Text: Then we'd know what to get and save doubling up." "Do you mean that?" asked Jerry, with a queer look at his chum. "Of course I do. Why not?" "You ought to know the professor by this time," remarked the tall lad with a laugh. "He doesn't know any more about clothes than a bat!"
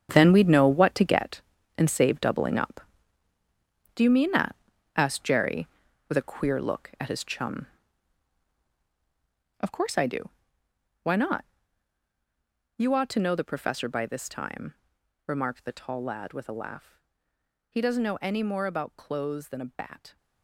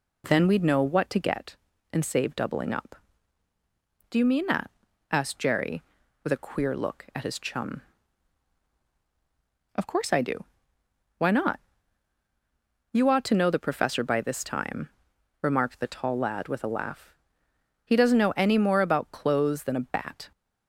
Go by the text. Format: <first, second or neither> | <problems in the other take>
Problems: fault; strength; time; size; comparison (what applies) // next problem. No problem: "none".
second | gets quieter; strong; throughout; 12 dB